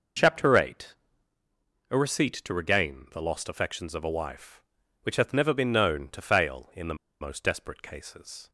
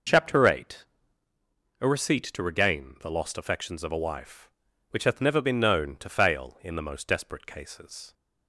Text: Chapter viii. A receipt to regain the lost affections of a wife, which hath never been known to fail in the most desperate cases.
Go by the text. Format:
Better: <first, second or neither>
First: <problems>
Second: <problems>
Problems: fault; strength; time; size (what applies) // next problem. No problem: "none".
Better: second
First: pauses between "the" and "most"; slight; at 6.9 s; 0.24 s long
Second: none